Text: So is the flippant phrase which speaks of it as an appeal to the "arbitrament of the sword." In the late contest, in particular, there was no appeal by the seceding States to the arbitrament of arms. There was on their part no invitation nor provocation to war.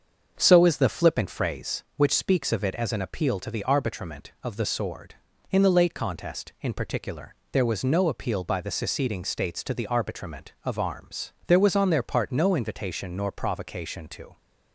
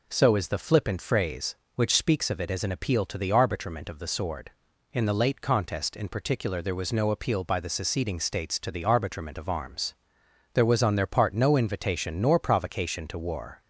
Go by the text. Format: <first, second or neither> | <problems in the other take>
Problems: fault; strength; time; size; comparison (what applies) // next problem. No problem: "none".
second | starts louder than the rest; until 1.3 s; 7 dB // stops before "war"; at 14.3 s